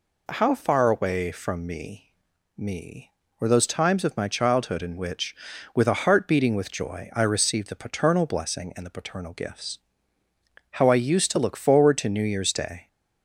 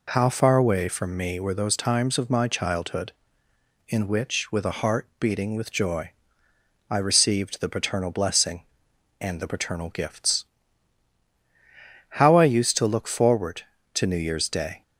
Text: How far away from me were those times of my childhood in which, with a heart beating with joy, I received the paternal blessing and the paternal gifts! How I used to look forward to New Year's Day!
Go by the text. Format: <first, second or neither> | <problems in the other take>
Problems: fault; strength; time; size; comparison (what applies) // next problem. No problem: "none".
second | says "me" twice; at 2.5 s